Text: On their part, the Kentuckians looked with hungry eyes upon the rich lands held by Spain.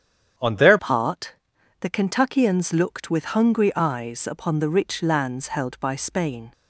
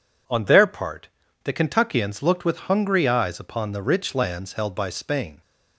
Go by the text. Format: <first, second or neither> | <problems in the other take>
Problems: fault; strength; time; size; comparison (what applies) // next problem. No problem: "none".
second | starts louder than the rest; strong; until 1.8 s; 8.5 dB // changes voice at "part"; from 0.7 s on; 5.8 s long